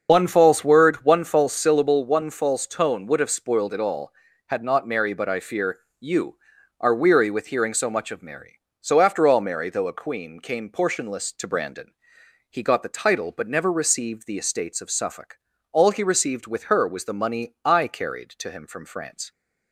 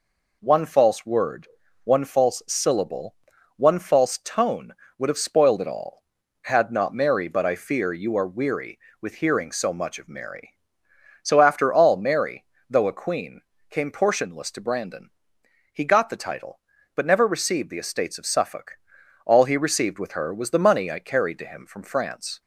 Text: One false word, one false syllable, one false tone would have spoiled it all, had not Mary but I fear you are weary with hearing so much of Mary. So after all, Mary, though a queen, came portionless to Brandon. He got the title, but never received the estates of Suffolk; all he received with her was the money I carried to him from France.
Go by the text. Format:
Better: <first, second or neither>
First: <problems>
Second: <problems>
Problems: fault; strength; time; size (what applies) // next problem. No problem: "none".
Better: second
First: loses the start of "One"; at 0.0 s; 45 ms // starts louder than the rest; until 1.1 s; 6.5 dB // pauses between "fear" and "you"; slight; at 5.7 s; 0.22 s long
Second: none